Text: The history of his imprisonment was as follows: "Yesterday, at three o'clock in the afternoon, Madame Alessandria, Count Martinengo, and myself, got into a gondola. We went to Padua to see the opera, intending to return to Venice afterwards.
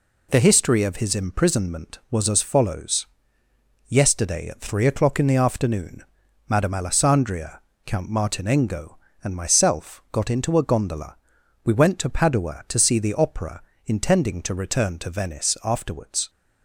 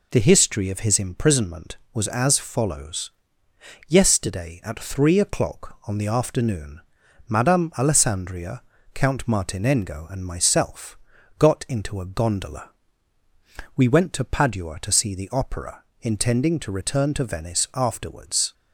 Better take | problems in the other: first | says "on" for "in"; at 5.8 s

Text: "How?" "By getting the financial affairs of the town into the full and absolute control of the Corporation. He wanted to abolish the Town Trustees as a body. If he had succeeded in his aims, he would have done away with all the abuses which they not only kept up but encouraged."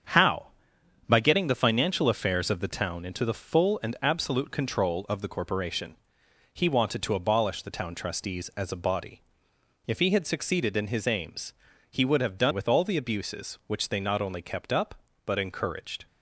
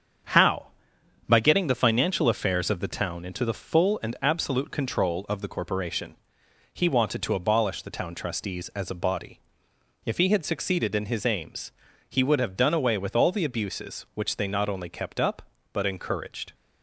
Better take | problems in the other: second | starts louder than the rest; strong; until 1.6 s; 7.5 dB; strong in the second // skips "away"; at 12.5 s

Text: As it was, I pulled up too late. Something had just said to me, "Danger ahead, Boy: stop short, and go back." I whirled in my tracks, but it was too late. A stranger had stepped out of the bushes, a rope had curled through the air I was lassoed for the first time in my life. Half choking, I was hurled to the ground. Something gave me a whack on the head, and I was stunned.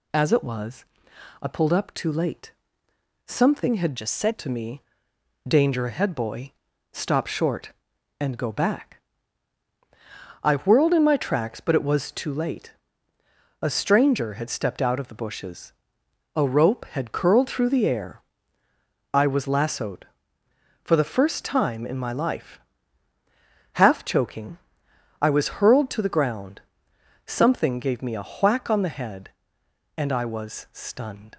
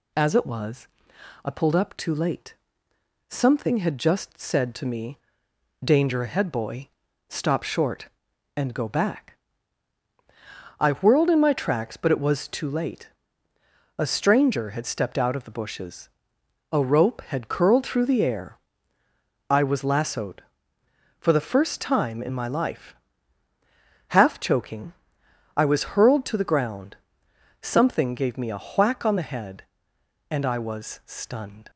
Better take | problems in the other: second | changes voice from "just" to "said"; from 3.9 to 4.3 s; 0.4 s long // pauses between "air" and "I"; noticeable; at 18.2 s; 0.92 s long; noticeable in the second

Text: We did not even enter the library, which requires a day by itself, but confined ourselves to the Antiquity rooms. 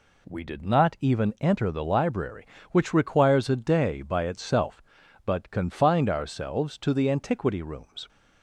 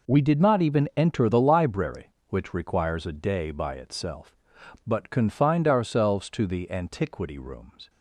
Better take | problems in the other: neither | none

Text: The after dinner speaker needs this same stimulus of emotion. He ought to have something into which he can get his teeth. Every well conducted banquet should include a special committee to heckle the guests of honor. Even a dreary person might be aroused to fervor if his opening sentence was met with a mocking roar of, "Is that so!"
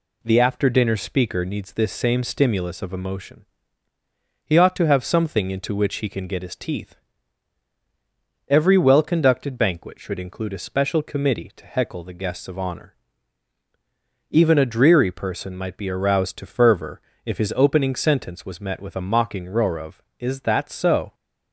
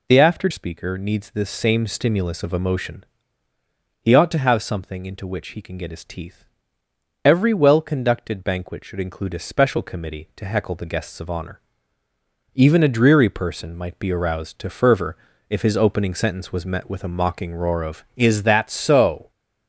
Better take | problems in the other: first | skips "dinner"; at 0.4 s // pauses between "fervor" and "if"; slight; at 15.1 s; 0.32 s long; slight in the first

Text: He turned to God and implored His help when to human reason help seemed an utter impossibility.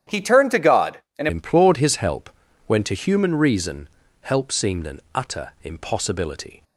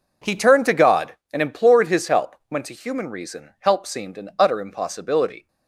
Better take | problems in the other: second | starts louder than the rest; strong; until 1.2 s; 10 dB // changes voice at "implored"; from 1.2 s on; 5.4 s long // pauses between "help" and "when"; at 2.2 s; 0.38 s long // pauses between "reason" and "help"; slight; at 3.8 s; 0.36 s long // pauses between "an" and "utter"; slight; at 4.9 s; 0.16 s long

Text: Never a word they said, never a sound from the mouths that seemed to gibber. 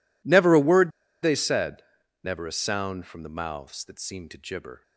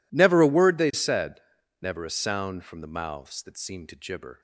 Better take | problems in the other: second | pauses between "word" and "they"; slight; at 0.9 s; 0.32 s long

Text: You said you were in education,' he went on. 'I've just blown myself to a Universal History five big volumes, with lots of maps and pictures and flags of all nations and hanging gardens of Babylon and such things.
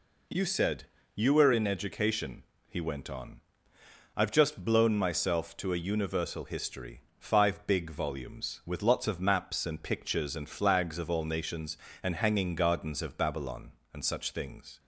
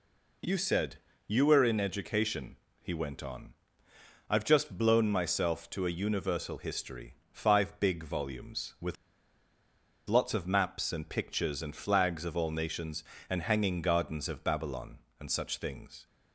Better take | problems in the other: first | pauses between "said" and "you"; slight; at 0.9 s; 0.28 s long; slight in the first // pauses between "History" and "five"; slight; at 7.1 s; 0.16 s long; slight in the first // pauses between "with" and "lots"; at 8.9 s; 1.1 s long

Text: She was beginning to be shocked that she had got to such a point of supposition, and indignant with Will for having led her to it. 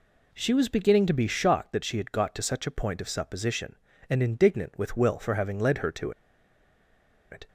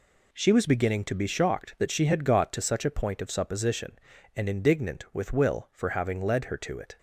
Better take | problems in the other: second | pauses between "to" and "it"; at 6.1 s; 1.1 s long

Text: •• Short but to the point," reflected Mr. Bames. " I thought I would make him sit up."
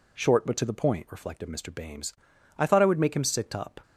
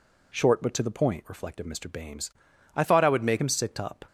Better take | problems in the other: first | changes voice from "thought" to "make"; from 2.8 to 3.3 s; 0.5 s long

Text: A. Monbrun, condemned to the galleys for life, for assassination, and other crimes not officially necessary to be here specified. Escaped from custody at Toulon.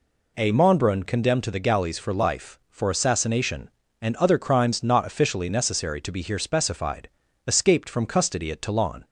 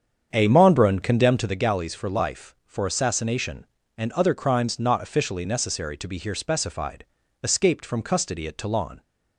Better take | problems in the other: first | starts louder than the rest; strong; until 1.7 s; 7.5 dB

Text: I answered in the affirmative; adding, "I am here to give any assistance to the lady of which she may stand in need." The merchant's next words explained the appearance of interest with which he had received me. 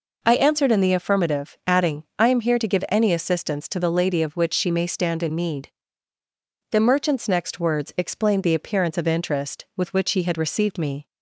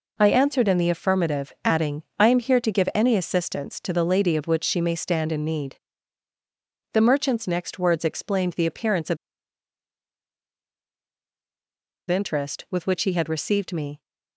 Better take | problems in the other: first | pauses between "of" and "interest"; strong; at 9.1 s; 2.9 s long

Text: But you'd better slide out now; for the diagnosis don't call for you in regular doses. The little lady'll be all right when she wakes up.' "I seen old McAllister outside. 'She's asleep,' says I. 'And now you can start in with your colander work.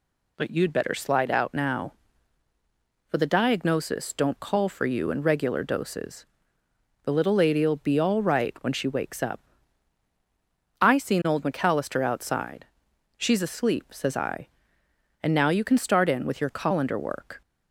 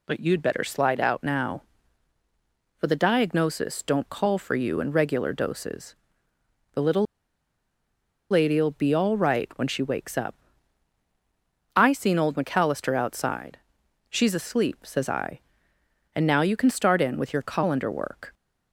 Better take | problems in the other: first | pauses between "little" and "lady'll"; strong; at 7.0 s; 1.2 s long

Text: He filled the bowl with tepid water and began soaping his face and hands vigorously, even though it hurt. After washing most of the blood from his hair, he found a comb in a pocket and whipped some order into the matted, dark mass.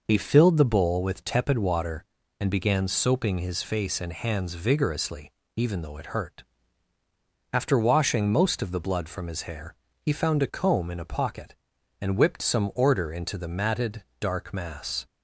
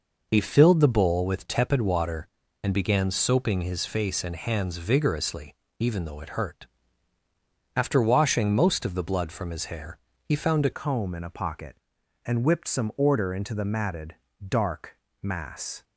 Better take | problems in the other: first | changes voice at "comb"; from 10.7 s on; 5.1 s long // pauses between "dark" and "mass"; slight; at 14.9 s; 0.24 s long

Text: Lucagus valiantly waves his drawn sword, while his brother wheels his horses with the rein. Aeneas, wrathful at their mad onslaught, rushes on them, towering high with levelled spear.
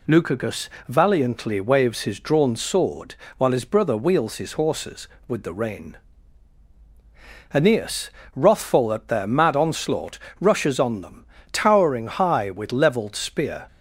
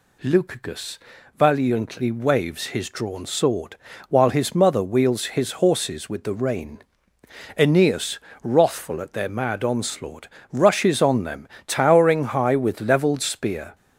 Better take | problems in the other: first | pauses between "Lucagus" and "valiantly"; at 0.9 s; 0.40 s long; slight in the first // says "mother" for "brother"; at 4.5 s

